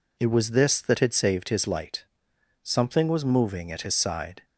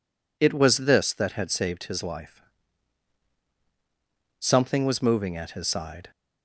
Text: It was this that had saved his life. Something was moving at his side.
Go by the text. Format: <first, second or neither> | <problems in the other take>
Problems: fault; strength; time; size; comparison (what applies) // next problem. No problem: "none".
second | says "light" for "life"; at 1.6 s